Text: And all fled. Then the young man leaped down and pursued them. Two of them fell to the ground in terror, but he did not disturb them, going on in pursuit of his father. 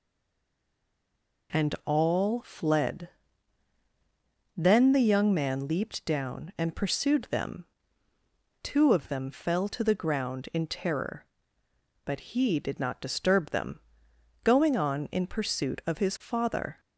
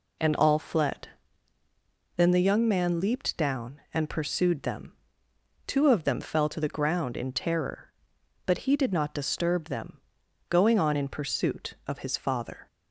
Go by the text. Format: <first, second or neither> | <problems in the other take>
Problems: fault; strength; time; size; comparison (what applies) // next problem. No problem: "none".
second | stays silent before the first word; noticeable; until 1.4 s; 1.4 s long